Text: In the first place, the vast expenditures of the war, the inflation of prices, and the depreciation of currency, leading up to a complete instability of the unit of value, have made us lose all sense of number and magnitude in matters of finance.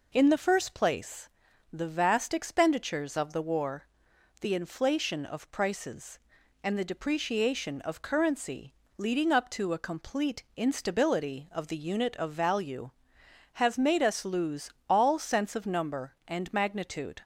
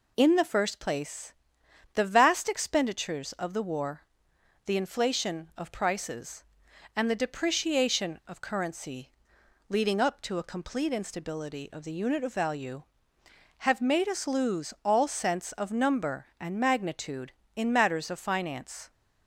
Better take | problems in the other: second | pauses between "lose" and "all"; slight; at 14.6 s; 0.18 s long // stops before "in matters of finance"; at 17.2 s

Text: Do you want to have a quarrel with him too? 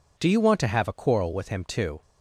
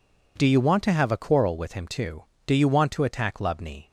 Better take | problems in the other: first | goes on to say "Do you want to attack Lubni"; from 2.4 s on; 1.4 s long

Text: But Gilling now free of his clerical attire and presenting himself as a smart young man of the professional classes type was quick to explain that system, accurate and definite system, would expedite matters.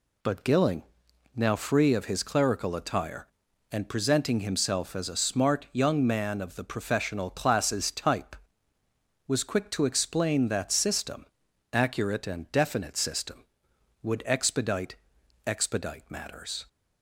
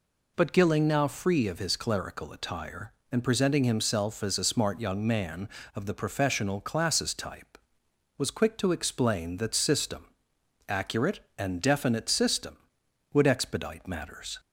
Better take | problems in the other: second | pauses between "Gilling" and "now"; noticeable; at 0.8 s; 0.52 s long // says "expedite" twice; at 15.4 s

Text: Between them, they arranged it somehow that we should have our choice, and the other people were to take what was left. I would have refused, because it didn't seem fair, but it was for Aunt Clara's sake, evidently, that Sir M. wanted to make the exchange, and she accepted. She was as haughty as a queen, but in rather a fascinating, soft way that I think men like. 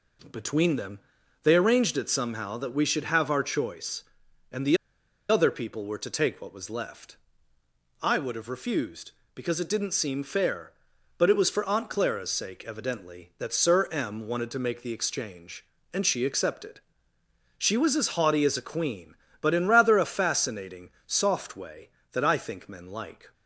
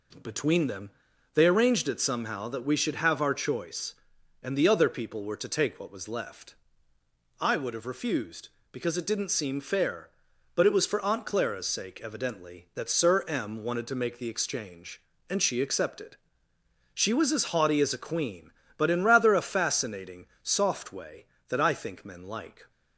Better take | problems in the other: second | pauses between "the" and "other"; noticeable; at 4.7 s; 0.53 s long

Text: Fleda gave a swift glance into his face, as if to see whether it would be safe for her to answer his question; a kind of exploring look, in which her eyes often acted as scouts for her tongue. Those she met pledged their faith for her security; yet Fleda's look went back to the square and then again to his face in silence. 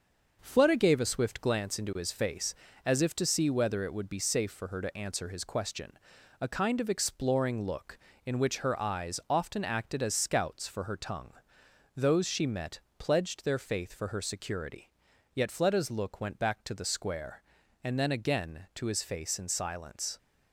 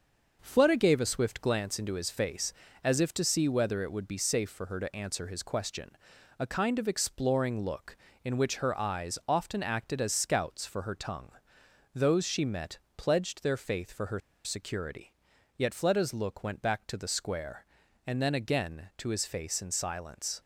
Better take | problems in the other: first | pauses between "met" and "pledged"; slight; at 12.7 s; 0.18 s long; slight in the first // pauses between "her" and "security"; slight; at 14.2 s; 0.24 s long

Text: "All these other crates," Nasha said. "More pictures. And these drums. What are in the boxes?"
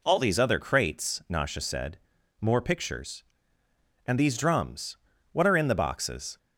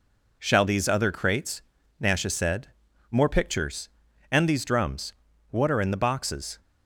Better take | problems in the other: first | says "Shall" for "All"; at 0.4 s

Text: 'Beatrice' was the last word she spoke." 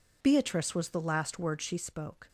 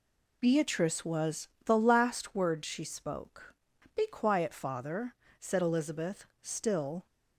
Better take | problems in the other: first | pauses between "was" and "the"; slight; at 1.4 s; 0.16 s long // goes on to say "Be quiet father said Elizabeth still"; strong; from 3.9 s on; 3.1 s long

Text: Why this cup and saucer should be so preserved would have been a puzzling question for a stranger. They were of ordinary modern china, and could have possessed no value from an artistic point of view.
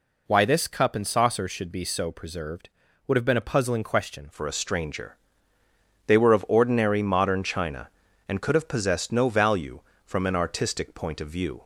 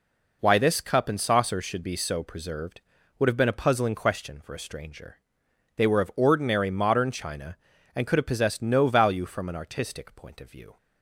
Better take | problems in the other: second | changes voice at "for"; from 4.3 s on; 7.3 s long

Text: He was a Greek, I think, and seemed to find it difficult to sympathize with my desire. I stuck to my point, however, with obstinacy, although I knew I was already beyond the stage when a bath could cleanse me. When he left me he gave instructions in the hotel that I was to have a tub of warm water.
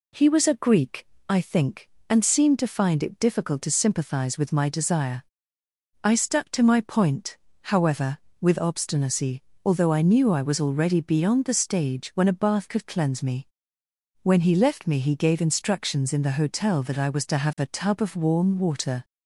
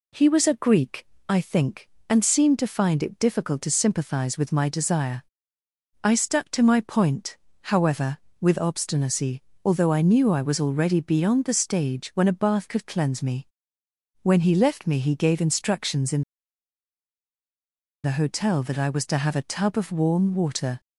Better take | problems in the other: first | pauses between "in" and "the"; strong; at 16.2 s; 1.8 s long

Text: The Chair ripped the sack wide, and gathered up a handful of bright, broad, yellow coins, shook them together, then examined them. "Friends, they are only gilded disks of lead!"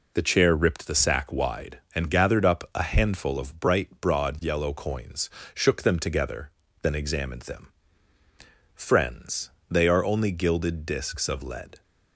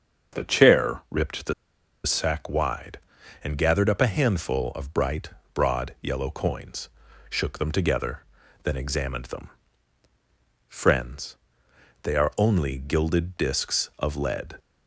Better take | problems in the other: first | starts louder than the rest; until 1.4 s; 6.5 dB // pauses between "the" and "sack"; noticeable; at 1.5 s; 0.50 s long

